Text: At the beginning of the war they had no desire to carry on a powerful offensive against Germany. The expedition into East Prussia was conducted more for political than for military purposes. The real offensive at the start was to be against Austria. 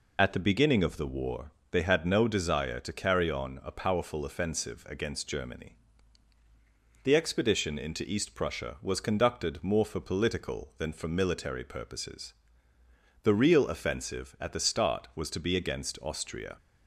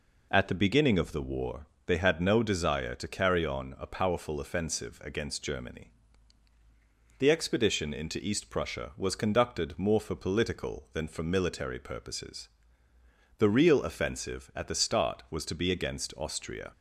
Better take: second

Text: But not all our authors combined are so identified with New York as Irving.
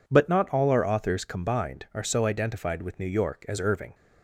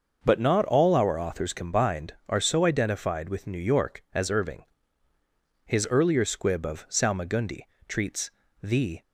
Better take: first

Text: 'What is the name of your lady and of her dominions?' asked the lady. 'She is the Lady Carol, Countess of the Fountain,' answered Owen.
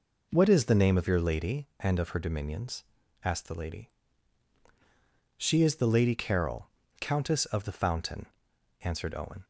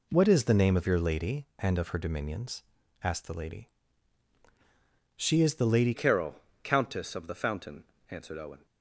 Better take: first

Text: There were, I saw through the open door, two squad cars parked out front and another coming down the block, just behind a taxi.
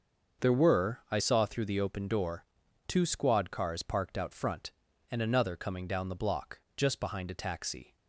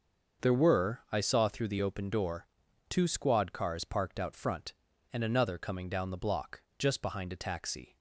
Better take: neither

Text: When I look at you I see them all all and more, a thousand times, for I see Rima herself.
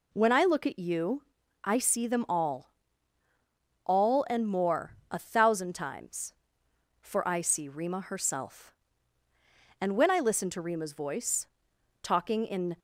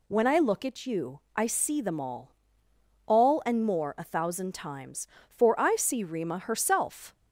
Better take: second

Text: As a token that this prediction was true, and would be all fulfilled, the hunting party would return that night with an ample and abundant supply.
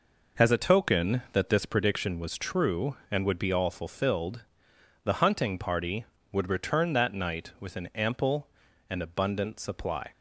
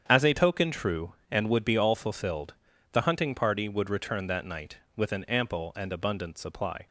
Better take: first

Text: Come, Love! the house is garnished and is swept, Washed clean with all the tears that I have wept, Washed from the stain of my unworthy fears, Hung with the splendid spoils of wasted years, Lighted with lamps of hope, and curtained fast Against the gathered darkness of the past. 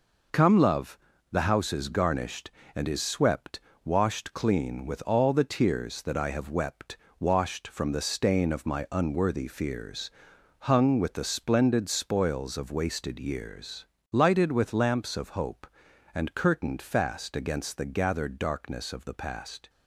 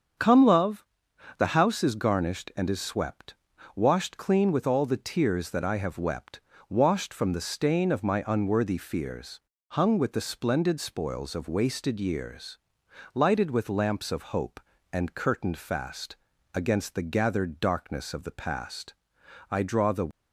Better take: first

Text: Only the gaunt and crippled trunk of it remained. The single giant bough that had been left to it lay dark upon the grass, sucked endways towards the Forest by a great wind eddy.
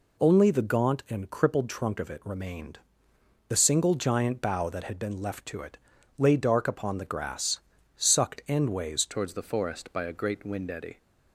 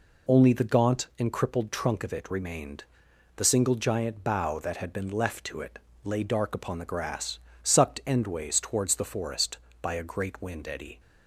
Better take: second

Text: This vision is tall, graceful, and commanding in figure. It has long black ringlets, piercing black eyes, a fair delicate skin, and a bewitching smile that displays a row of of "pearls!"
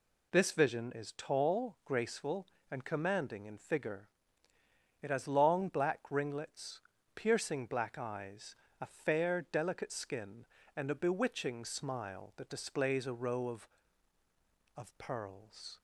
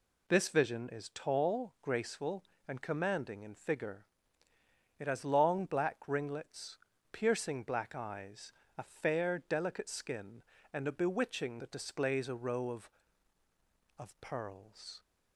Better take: first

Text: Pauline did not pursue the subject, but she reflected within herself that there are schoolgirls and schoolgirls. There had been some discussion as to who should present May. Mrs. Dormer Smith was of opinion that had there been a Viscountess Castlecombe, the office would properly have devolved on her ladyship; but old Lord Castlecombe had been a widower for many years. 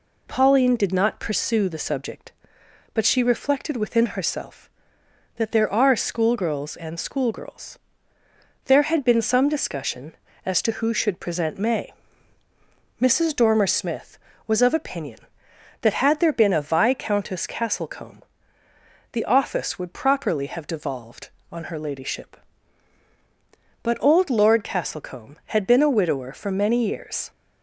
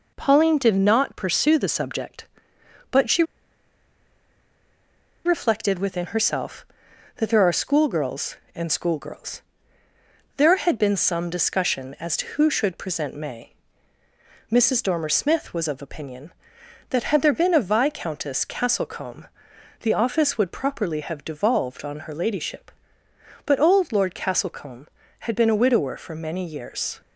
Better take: first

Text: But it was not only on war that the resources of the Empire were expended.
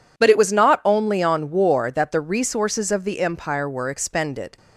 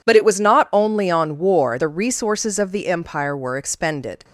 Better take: first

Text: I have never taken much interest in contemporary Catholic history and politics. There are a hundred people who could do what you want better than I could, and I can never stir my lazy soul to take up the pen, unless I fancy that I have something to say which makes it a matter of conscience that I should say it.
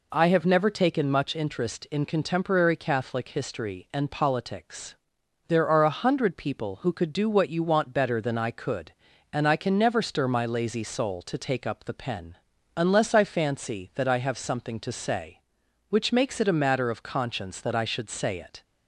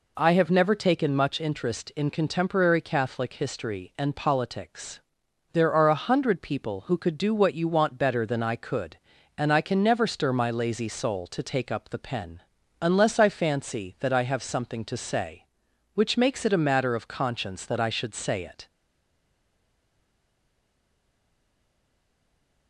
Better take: first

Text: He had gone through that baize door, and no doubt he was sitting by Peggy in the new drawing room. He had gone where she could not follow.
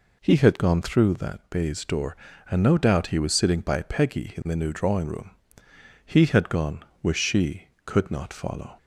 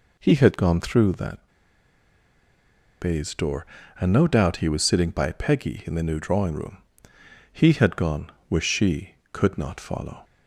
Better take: first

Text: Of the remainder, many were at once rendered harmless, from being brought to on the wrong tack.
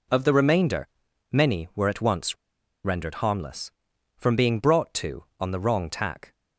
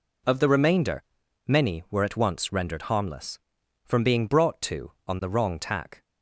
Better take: second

